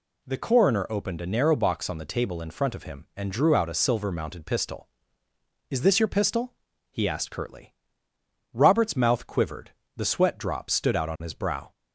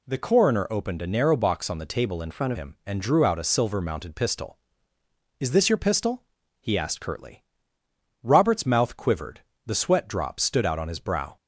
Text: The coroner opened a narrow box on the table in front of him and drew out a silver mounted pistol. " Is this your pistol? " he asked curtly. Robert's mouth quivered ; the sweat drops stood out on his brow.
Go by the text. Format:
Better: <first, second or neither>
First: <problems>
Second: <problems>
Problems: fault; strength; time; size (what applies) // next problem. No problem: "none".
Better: first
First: none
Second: changes voice from "front" to "of"; from 2.2 to 2.5 s; 0.3 s long